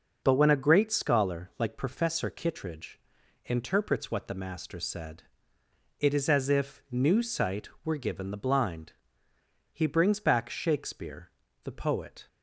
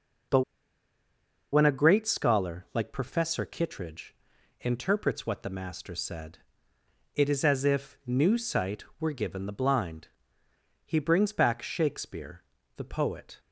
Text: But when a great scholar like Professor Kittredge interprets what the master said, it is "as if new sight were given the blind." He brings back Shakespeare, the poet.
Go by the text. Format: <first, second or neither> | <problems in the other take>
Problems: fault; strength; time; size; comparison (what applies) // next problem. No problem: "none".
first | pauses between "But" and "when"; at 0.4 s; 1.1 s long // pauses between "Kittredge" and "interprets"; noticeable; at 4.1 s; 0.46 s long; noticeable in the first